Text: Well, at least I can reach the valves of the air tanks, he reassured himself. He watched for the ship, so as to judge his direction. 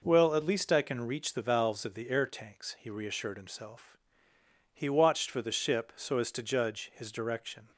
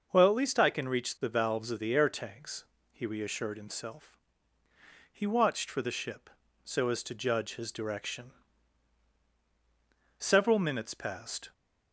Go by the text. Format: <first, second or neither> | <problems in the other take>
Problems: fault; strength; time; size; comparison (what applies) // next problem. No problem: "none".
first | starts louder than the rest; until 1.1 s; 6 dB // goes on to say "Several minutes passed"; from 10.1 s on; 1.3 s long